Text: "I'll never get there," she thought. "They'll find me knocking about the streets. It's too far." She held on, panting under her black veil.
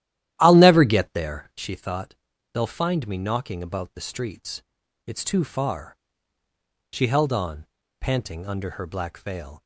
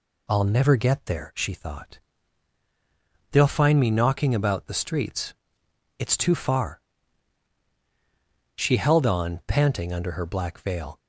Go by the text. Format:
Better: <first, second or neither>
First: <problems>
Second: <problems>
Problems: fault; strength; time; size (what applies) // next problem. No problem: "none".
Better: second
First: starts louder than the rest; strong; until 1.7 s; 13 dB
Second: none